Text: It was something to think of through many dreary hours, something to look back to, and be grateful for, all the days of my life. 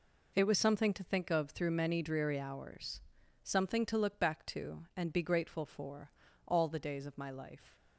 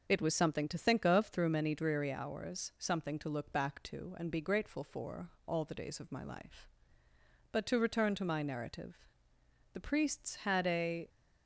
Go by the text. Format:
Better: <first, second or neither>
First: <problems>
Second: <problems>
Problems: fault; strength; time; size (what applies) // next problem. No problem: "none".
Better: first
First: none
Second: goes on to say "But to return to my narrative The priests had a"; strong; from 7.5 s on; 3.5 s long